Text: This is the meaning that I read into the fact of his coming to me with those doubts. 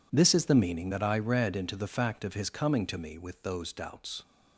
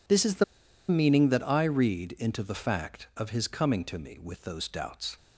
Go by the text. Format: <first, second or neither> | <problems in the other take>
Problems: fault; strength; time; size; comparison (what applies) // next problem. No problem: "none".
first | pauses between "the" and "meaning"; at 0.4 s; 0.45 s long